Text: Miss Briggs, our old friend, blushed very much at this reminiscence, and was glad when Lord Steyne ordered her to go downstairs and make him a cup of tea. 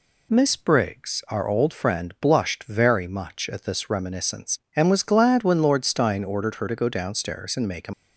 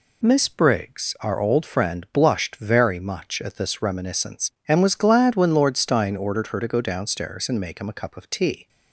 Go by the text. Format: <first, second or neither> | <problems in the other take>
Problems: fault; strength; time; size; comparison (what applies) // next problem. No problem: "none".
second | stops before "a cup of tea"; at 7.9 s